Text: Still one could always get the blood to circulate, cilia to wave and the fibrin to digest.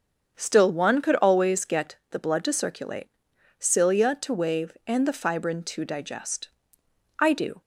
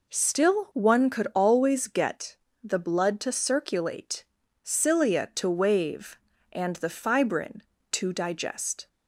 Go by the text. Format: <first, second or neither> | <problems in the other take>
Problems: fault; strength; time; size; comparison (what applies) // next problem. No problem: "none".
second | starts louder than the rest; strong; until 1.3 s; 7 dB // pauses between "get" and "the"; slight; at 1.9 s; 0.16 s long; slight in the second // goes on to say "I do"; slight; from 7.1 s on; 0.42 s long